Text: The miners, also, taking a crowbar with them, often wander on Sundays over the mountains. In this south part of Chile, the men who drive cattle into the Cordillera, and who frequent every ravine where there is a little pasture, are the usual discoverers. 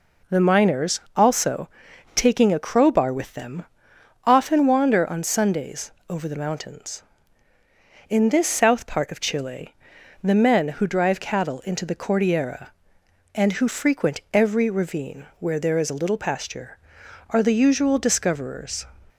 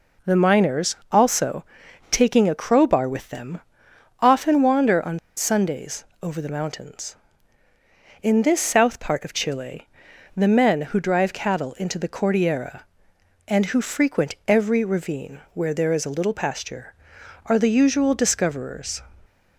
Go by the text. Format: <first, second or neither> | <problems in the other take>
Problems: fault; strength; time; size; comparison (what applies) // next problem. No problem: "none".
first | pauses between "on" and "Sundays"; slight; at 5.1 s; 0.18 s long // pauses between "Sundays" and "over"; slight; at 6.0 s; 0.18 s long; slight in the first // pauses between "ravine" and "where"; slight; at 15.3 s; 0.16 s long; slight in the first